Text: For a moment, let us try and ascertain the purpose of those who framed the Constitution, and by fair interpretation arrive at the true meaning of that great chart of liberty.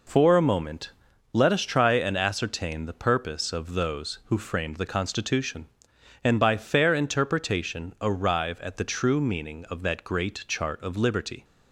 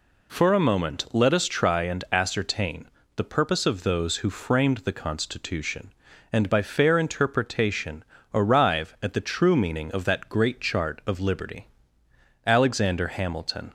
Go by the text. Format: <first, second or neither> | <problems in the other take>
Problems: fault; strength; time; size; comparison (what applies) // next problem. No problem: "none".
first | pauses between "ascertain" and "the"; slight; at 2.8 s; 0.30 s long // pauses between "interpretation" and "arrive"; slight; at 8.0 s; 0.28 s long // goes on to say "Alexander Hamilton"; noticeable; from 12.4 s on; 1.2 s long